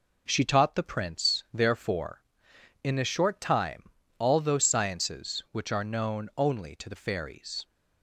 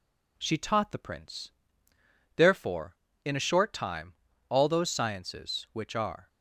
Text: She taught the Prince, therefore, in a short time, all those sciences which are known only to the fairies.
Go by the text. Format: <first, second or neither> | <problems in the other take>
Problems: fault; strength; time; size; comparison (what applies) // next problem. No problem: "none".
first | stops before "known only to the fairies"; at 6.2 s